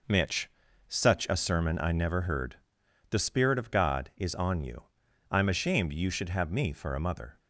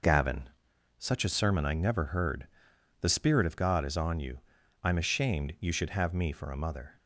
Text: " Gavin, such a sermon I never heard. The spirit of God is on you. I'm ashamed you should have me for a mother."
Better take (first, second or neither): second